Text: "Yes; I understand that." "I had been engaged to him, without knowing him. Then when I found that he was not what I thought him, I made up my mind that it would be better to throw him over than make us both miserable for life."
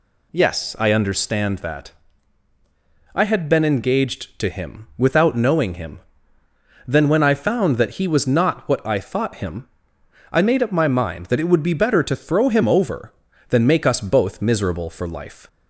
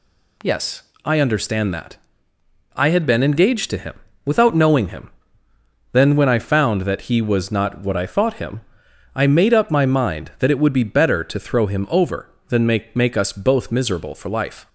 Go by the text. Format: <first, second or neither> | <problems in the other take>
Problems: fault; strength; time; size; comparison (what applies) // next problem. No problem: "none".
first | says "make" twice; at 12.9 s